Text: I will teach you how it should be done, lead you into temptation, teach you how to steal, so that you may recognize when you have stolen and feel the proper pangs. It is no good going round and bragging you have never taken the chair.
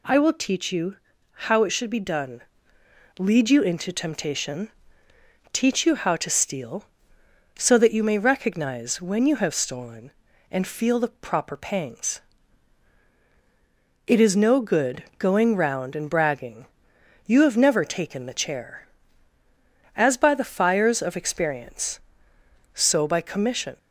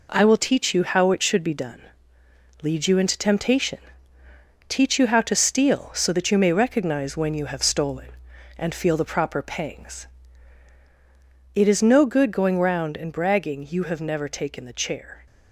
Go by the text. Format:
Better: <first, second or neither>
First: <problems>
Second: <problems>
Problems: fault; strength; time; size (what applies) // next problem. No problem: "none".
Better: second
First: pauses between "you" and "how"; slight; at 0.9 s; 0.36 s long // pauses between "bragging" and "you"; noticeable; at 16.6 s; 0.60 s long // goes on to say "As by the fires of experience so by commission"; strong; from 19.9 s on; 3.8 s long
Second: none